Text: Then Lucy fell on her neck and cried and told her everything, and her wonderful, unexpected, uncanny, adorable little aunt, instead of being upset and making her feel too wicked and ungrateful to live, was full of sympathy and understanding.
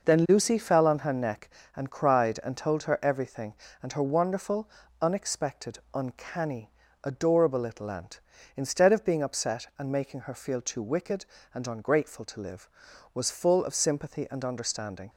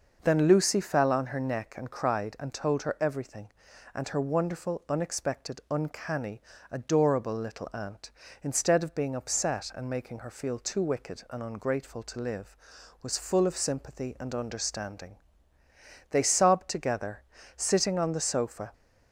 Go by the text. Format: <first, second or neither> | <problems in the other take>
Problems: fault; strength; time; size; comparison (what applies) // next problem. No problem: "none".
first | goes on to say "They sobbed together sitting on the sofa"; strong; from 16.1 s on; 2.6 s long